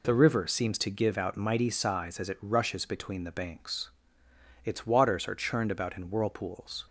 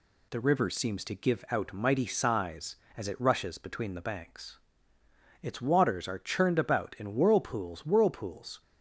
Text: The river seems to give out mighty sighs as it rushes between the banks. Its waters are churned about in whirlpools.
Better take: first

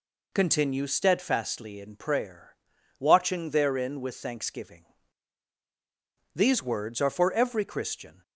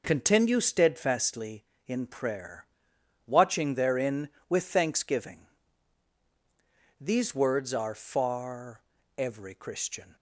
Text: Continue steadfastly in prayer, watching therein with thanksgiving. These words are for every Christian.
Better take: first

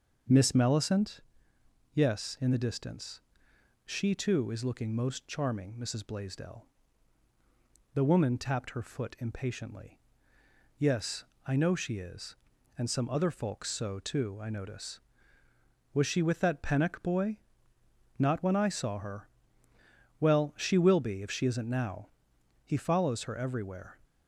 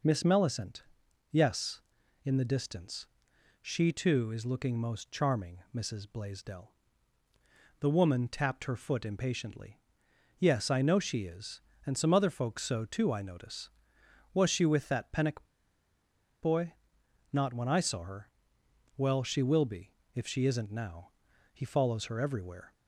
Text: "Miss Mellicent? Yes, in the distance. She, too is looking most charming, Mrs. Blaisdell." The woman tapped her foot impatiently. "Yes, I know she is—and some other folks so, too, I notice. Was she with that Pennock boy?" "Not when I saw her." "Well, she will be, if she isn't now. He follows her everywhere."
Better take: first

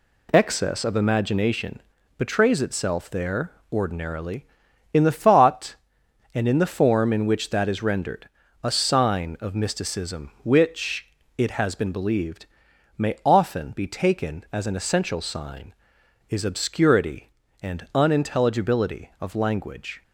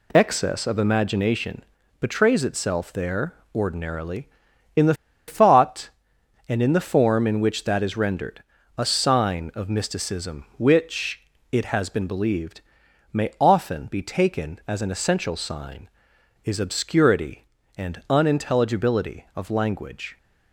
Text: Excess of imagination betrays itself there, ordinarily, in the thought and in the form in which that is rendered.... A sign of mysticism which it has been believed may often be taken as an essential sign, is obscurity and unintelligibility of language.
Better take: first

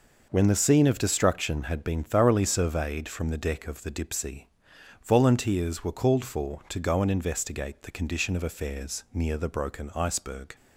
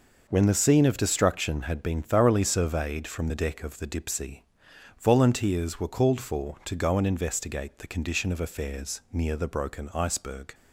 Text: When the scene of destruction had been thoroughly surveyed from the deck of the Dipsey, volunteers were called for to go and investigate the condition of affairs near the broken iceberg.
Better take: neither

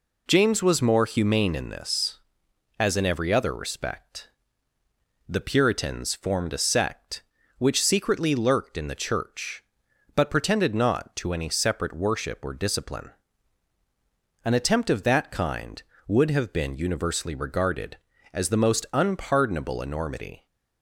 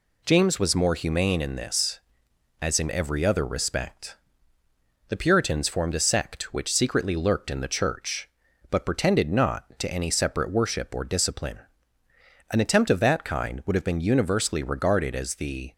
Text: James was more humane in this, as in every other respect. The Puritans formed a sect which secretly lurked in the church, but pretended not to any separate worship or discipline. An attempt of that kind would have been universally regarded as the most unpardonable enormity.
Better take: first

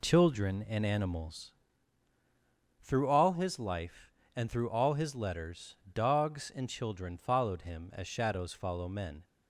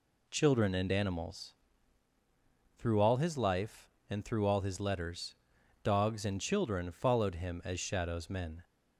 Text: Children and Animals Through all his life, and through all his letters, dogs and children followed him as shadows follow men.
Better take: first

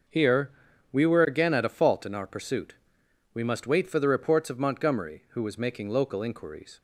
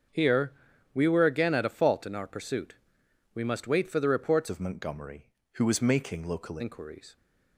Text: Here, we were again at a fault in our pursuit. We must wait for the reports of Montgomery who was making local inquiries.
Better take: first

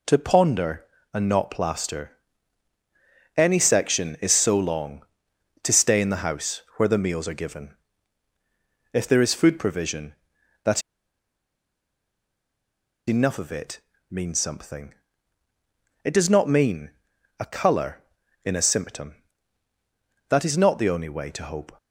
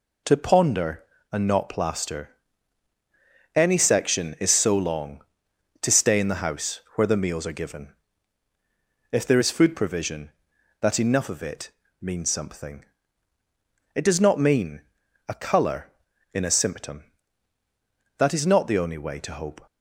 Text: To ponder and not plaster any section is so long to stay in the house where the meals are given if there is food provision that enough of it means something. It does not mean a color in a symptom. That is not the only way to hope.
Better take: second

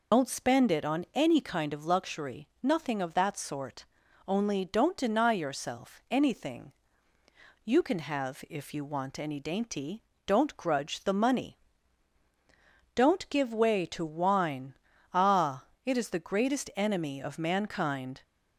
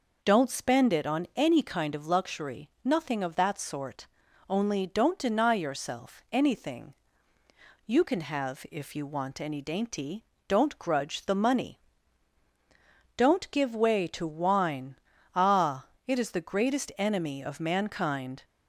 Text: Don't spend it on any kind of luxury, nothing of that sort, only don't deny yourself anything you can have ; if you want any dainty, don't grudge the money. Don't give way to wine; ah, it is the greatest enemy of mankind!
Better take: second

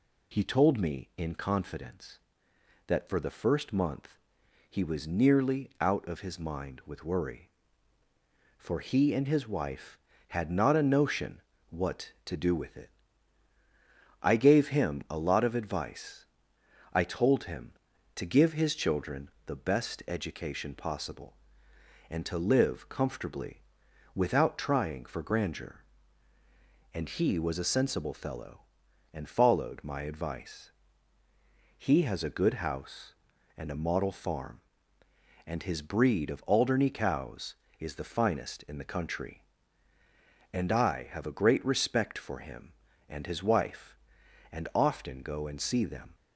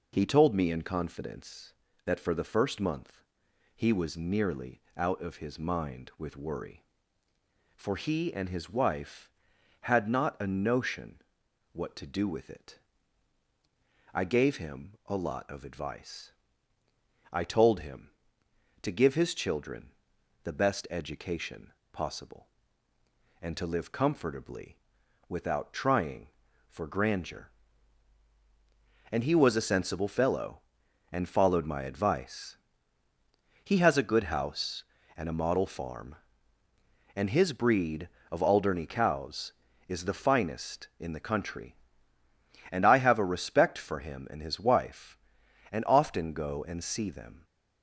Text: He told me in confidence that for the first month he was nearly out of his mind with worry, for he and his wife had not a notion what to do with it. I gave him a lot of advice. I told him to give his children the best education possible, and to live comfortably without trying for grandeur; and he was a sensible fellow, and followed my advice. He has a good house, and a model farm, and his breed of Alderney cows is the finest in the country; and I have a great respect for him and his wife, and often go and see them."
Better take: first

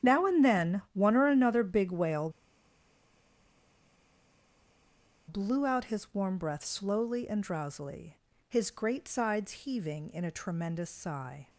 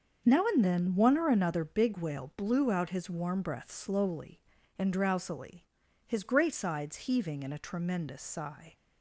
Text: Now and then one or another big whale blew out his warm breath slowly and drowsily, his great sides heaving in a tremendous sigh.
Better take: second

